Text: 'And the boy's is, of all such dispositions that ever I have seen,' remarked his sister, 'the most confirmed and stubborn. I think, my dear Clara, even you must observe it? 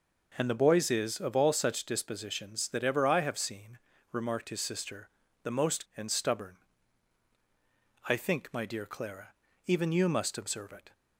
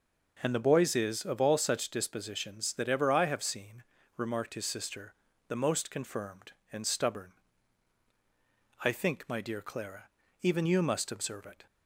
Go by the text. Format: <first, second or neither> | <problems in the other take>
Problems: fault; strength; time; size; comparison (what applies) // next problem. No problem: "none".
second | skips "confirmed"; at 5.9 s